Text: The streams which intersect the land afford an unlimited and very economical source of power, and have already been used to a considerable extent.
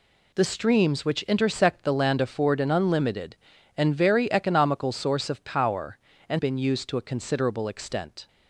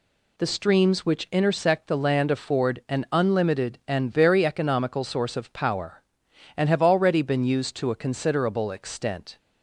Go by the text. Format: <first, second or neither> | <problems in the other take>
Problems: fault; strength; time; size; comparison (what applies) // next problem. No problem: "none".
second | skips "have already"; at 6.3 s